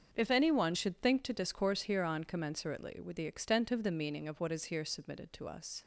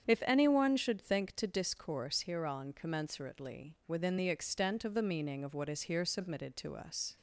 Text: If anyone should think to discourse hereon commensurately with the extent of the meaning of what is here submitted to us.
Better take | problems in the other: first | starts louder than the rest; strong; until 1.1 s; 8 dB; also in the first // says "within" for "with"; at 3.8 s

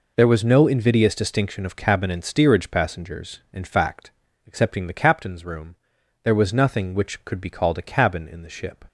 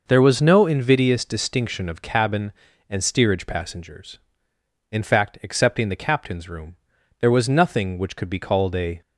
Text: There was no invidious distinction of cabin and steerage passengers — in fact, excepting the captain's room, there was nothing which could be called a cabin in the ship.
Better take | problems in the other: first | stops before "cabin in the ship"; at 9.0 s

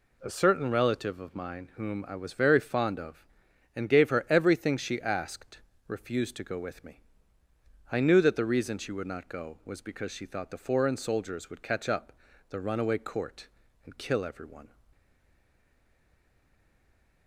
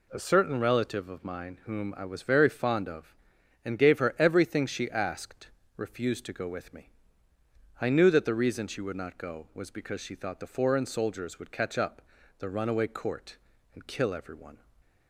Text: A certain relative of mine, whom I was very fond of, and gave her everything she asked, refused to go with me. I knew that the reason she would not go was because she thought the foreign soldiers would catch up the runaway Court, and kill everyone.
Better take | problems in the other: second | pauses between "up" and "the"; at 12.1 s; 0.38 s long; also in the second // stays silent after the last word; from 14.9 s on; 2.3 s long

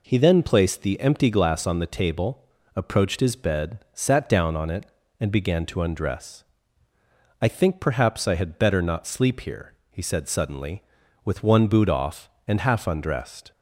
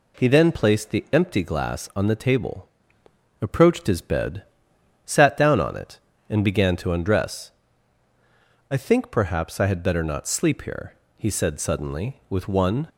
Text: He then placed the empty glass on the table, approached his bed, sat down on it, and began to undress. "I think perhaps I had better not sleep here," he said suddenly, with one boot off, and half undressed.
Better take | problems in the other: first | stops before "boot off and half undressed"; at 12.8 s

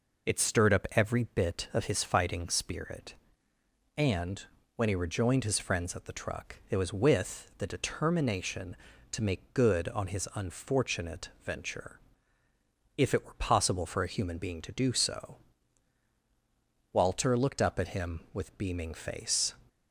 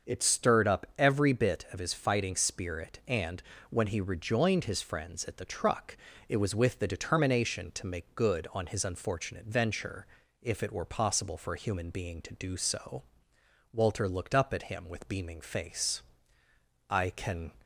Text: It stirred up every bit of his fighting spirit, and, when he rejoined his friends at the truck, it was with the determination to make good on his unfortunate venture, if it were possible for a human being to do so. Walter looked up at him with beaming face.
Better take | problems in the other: first | starts louder than the rest; until 1.1 s; 6.5 dB // goes on to say "I can"; noticeable; from 16.8 s on; 0.64 s long

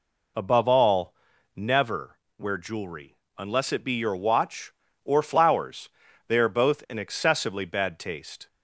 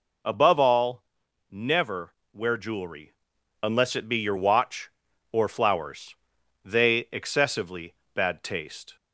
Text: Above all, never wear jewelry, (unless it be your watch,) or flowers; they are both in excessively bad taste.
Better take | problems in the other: first | pauses between "never" and "wear"; slight; at 2.1 s; 0.20 s long; slight in the first // skips "are both in"; at 7.0 s // pauses between "excessively" and "bad"; slight; at 7.9 s; 0.22 s long

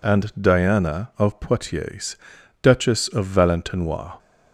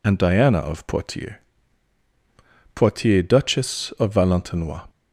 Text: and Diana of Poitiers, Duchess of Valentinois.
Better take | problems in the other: first | says "Poitiers" twice; at 2.7 s

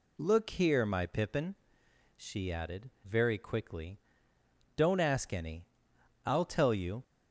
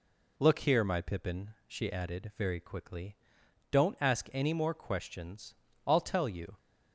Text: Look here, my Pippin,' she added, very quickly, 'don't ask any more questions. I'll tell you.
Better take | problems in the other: second | skips "more questions"; at 5.9 s

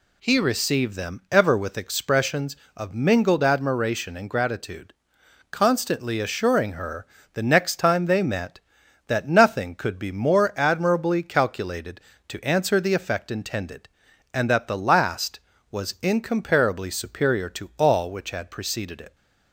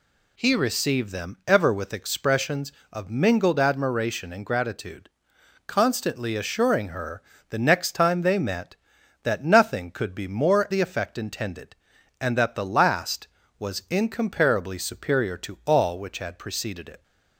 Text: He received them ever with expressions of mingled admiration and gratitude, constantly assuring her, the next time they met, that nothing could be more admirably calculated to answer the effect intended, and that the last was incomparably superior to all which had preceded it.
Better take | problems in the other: first | skips "admirably calculated to answer"; at 10.6 s

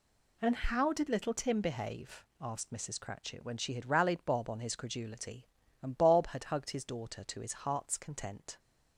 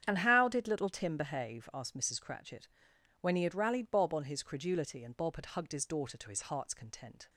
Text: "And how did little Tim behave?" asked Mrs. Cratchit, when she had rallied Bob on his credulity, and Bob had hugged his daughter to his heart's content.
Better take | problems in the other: first | starts louder than the rest; strong; until 1.0 s; 9 dB // says "he" for "she"; at 3.3 s

